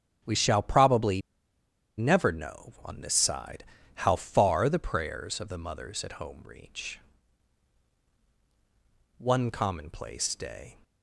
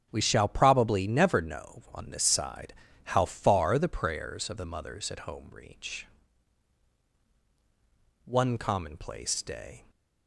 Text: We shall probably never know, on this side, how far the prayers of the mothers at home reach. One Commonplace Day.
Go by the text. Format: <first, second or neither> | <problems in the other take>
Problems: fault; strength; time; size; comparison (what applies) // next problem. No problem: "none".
second | starts louder than the rest; strong; until 2.0 s; 9 dB; strong in the second // pauses between "probably" and "never"; noticeable; at 1.2 s; 0.77 s long